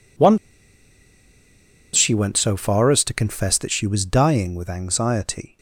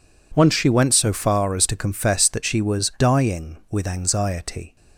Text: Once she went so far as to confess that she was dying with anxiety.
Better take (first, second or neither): second